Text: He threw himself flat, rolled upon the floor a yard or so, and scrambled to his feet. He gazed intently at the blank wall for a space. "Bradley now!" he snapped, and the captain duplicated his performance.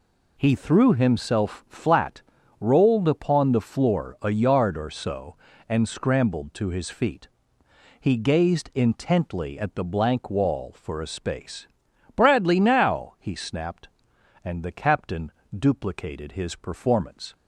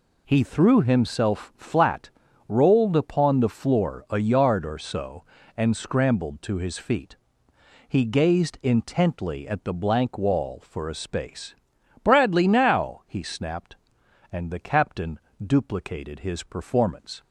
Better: neither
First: pauses between "captain" and "duplicated"; slight; at 15.3 s; 0.28 s long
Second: pauses between "captain" and "duplicated"; slight; at 15.1 s; 0.28 s long

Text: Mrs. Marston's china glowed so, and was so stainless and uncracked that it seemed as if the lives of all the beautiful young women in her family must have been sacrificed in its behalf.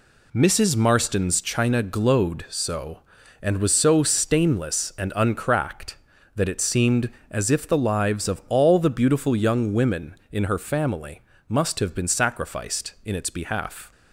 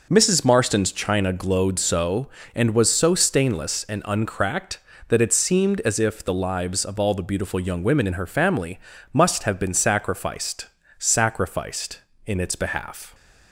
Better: first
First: pauses between "family" and "must"; slight; at 11.2 s; 0.28 s long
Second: pauses between "family" and "must"; slight; at 8.7 s; 0.34 s long // says "sacrificed" twice; at 11.0 s

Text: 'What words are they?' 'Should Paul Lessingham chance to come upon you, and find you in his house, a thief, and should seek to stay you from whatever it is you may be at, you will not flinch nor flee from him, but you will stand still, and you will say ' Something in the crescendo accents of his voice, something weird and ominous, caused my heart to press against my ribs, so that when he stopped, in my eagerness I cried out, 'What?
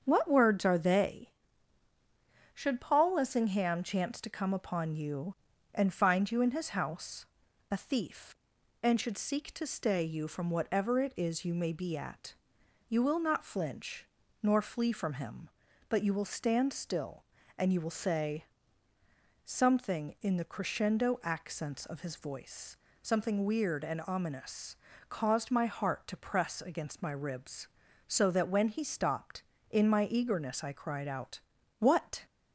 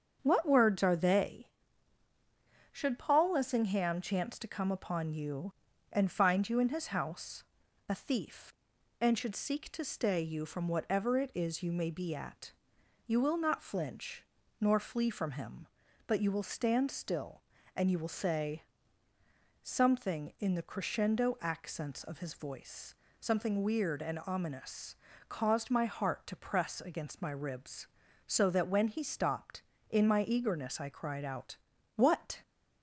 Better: neither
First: starts louder than the rest; strong; until 1.0 s; 7.5 dB // pauses between "flinch" and "nor"; slight; at 14.0 s; 0.36 s long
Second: starts louder than the rest; strong; until 1.2 s; 7.5 dB // pauses between "flinch" and "nor"; slight; at 14.2 s; 0.36 s long

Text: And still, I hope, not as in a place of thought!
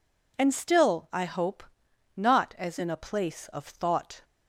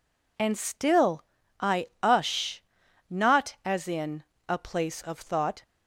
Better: first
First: none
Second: says "ush" for "hope"; at 2.0 s // pauses between "in" and "a"; slight; at 4.2 s; 0.24 s long

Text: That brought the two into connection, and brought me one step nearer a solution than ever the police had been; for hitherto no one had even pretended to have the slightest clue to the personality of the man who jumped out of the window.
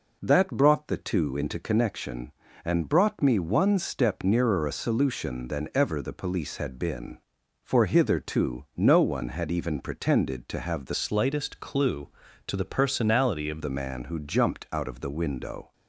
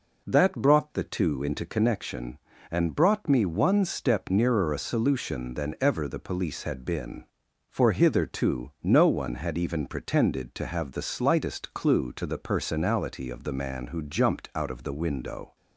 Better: second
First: changes voice from "slightest" to "of"; from 10.9 to 13.6 s; 2.7 s long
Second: none

